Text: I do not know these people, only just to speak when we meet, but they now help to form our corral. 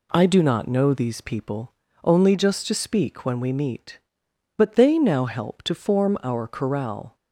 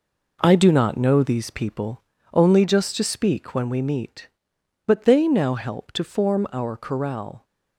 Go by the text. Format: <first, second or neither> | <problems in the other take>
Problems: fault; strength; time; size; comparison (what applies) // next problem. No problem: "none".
first | gets quieter; strong; throughout; 7.5 dB